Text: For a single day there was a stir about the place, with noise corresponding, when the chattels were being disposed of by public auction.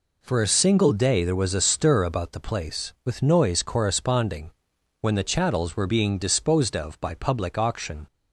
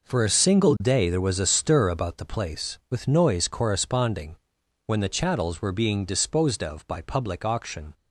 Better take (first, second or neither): first